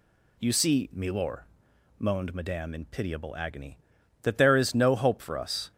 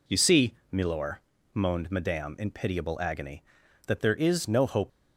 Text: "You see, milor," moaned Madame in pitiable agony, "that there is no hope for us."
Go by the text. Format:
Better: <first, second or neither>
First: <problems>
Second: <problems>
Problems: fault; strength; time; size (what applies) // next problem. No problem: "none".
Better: first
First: none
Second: stops before "for us"; at 4.8 s